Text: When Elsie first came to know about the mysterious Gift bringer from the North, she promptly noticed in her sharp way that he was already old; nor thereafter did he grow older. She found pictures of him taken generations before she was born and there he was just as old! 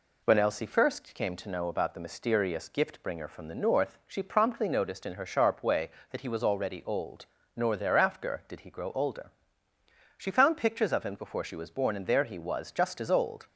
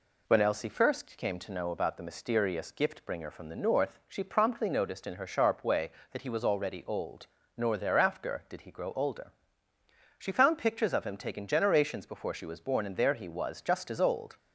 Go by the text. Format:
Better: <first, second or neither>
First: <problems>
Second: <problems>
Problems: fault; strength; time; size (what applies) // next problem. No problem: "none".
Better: second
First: skips "taken generations"; at 11.1 s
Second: none